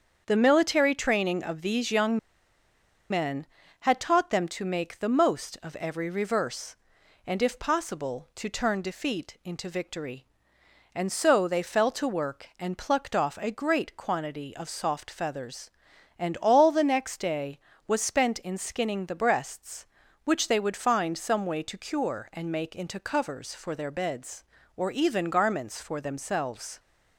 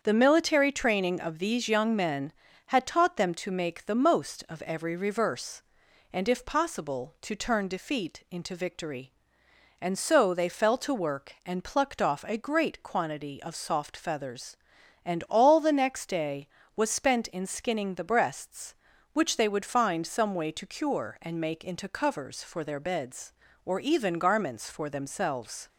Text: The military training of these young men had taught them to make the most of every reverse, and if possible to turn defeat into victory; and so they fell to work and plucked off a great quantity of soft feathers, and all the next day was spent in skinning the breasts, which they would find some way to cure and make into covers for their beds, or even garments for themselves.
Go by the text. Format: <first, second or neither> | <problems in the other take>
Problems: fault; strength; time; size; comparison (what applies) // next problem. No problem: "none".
second | starts louder than the rest; strong; until 1.2 s; 7.5 dB; strong in the second // pauses between "young" and "men"; noticeable; at 2.1 s; 0.93 s long